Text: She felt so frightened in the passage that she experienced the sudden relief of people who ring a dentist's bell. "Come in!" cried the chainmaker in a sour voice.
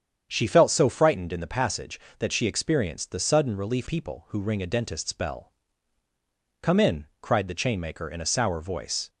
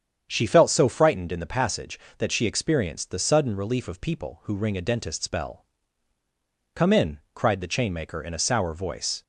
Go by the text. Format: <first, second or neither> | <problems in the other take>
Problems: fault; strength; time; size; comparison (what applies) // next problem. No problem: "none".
second | starts louder than the rest; strong; until 1.3 s; 8 dB; strong in the second // skips "of"; at 3.8 s